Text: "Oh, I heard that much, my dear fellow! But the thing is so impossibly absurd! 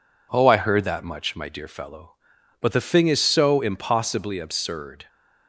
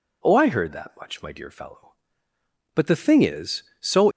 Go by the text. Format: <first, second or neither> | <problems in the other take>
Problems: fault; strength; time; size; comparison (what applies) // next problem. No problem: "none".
first | stops before "impossibly absurd"; at 4.1 s